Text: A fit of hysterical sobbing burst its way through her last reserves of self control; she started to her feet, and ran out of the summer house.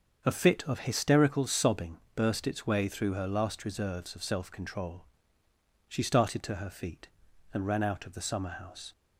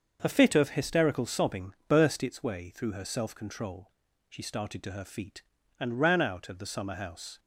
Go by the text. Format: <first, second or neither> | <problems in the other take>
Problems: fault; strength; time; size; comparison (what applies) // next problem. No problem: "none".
first | starts louder than the rest; until 1.2 s; 6.5 dB; also in the first // pauses between "sobbing" and "burst"; slight; at 1.7 s; 0.16 s long; slight in the first // skips "last reserves of"; at 3.0 s